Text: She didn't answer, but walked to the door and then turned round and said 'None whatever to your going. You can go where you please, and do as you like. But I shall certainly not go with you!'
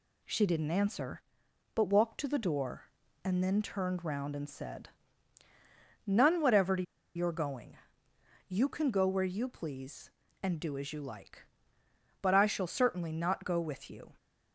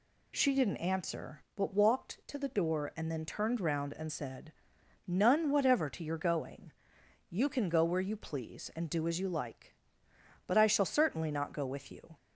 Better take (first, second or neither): second